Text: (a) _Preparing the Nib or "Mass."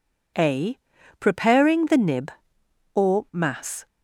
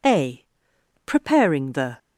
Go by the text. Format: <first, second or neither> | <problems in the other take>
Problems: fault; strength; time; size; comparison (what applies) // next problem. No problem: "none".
first | stops before "Nib or Mass"; at 1.9 s